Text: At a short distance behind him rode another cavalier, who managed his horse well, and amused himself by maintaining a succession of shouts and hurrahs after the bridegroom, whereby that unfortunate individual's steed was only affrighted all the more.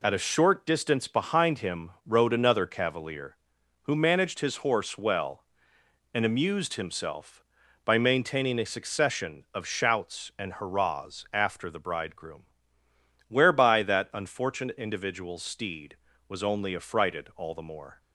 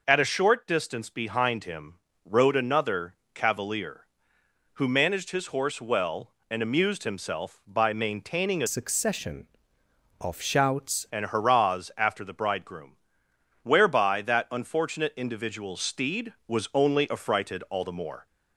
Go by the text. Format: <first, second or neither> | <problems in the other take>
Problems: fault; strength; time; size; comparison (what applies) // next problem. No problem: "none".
first | pauses between "him" and "rode"; slight; at 1.9 s; 0.32 s long // pauses between "another" and "cavalier"; slight; at 3.1 s; 0.20 s long // changes voice from "succession" to "shouts"; from 8.6 to 11.0 s; 2.4 s long